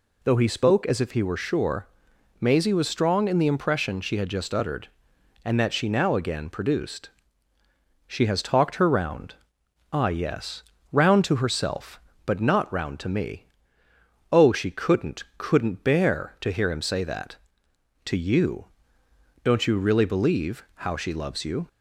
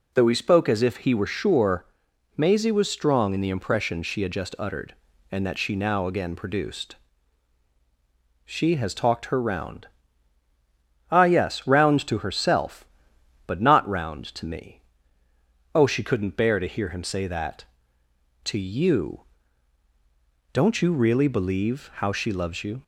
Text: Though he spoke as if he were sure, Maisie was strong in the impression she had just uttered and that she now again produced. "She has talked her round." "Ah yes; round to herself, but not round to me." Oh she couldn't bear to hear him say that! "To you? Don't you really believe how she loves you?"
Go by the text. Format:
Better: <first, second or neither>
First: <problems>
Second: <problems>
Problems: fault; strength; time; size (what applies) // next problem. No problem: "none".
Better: second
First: says "couldn't" twice; at 15.3 s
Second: none